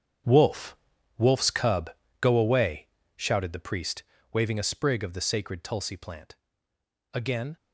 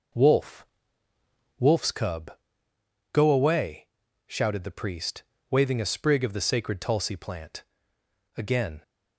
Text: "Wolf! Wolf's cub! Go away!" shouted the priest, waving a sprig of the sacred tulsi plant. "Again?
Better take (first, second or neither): second